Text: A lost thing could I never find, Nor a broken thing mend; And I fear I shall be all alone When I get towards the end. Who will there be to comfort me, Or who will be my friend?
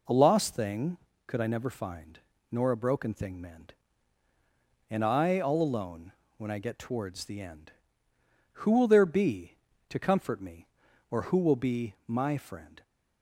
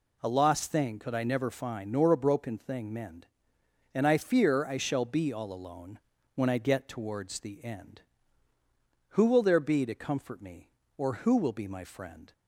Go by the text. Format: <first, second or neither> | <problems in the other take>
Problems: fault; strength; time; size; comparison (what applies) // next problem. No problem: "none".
second | skips "fear I shall be"; at 5.4 s // pauses between "alone" and "When"; slight; at 6.1 s; 0.24 s long; slight in the second